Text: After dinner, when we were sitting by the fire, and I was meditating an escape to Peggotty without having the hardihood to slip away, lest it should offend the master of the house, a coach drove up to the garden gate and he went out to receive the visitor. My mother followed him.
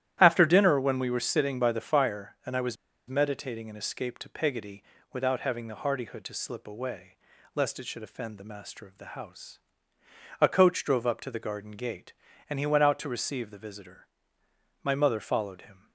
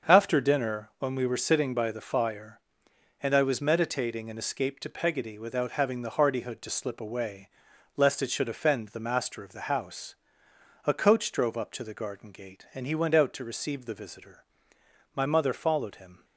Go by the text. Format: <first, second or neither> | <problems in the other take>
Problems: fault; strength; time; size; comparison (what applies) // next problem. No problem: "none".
second | starts louder than the rest; strong; until 1.2 s; 12 dB; also in the second // pauses between "was" and "meditating"; slight; at 2.7 s; 0.32 s long // pauses between "Peggotty" and "without"; slight; at 4.8 s; 0.30 s long